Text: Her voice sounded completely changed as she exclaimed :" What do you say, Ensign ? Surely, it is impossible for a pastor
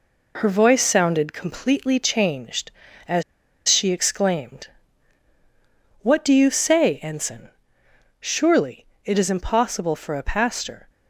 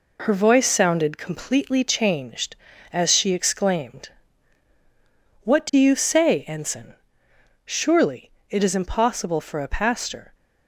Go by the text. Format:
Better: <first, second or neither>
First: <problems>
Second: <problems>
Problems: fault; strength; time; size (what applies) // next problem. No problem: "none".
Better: second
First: pauses between "as" and "she"; noticeable; at 3.2 s; 0.45 s long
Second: none